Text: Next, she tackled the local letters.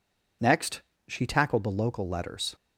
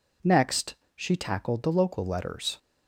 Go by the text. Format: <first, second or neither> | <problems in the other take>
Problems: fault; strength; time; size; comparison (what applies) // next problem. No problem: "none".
neither | none